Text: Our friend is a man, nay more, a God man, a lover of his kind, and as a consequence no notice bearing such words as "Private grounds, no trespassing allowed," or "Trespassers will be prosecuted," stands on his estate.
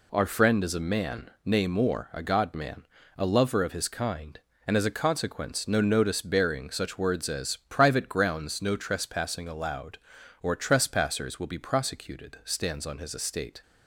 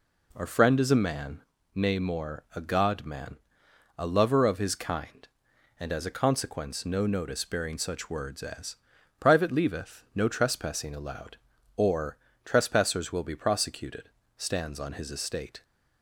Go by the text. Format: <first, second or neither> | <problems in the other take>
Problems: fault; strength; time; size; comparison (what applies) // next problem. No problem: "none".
first | pauses between "as" and "Private"; at 8.7 s; 0.42 s long // says "leaveth" for "grounds"; at 9.5 s // pauses between "or" and "Trespassers"; slight; at 12.1 s; 0.30 s long